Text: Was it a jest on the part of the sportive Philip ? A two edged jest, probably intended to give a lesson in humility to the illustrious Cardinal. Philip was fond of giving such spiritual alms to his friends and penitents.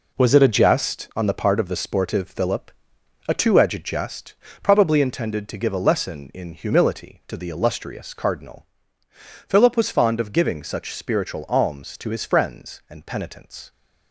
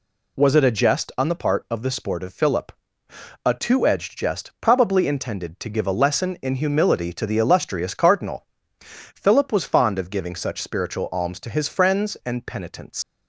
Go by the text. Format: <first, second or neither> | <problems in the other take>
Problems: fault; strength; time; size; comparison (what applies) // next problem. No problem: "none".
first | leaves "penitents" unfinished; at 13.0 s; 115 ms